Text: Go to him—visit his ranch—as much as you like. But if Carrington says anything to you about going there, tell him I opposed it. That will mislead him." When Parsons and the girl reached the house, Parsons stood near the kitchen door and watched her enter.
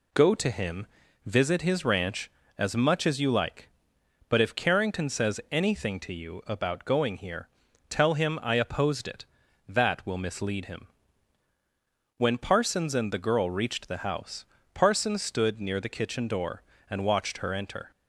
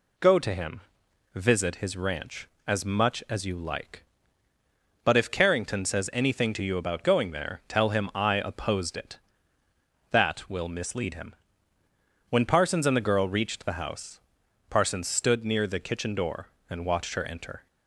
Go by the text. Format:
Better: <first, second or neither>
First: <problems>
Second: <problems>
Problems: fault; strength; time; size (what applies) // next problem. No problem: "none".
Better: second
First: says "here" for "there"; at 7.1 s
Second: none